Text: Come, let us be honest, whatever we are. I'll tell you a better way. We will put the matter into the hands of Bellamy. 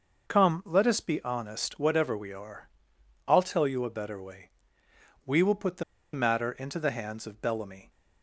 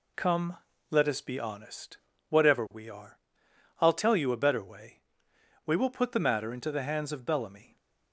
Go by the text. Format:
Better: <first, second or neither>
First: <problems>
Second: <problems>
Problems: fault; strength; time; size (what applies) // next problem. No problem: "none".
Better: second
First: pauses between "the" and "matter"; slight; at 5.8 s; 0.30 s long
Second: none